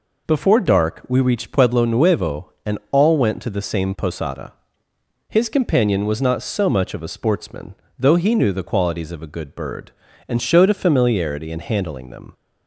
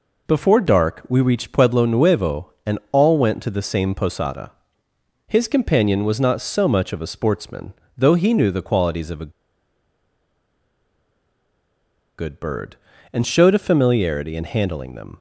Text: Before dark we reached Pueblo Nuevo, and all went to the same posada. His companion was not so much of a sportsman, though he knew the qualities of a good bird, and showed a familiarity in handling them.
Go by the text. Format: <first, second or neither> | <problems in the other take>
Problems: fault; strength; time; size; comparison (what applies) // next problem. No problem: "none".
first | pauses between "a" and "good"; strong; at 9.3 s; 2.8 s long